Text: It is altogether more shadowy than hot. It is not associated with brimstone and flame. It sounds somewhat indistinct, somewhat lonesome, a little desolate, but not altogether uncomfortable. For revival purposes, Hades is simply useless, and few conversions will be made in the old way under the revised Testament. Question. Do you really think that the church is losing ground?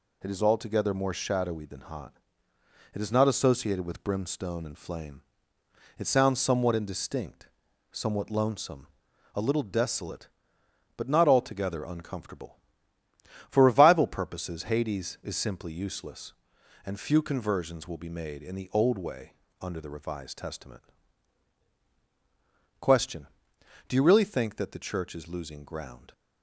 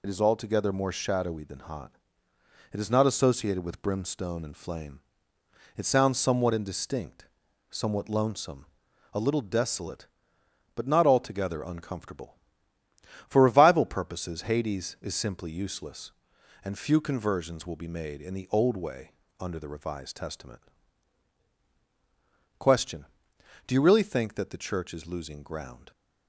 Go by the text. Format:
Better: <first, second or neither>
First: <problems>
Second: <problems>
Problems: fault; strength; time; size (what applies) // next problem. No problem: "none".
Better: first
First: pauses between "way" and "under"; slight; at 19.3 s; 0.28 s long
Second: loses the start of "It"; at 0.0 s; 35 ms // pauses between "way" and "under"; slight; at 19.1 s; 0.28 s long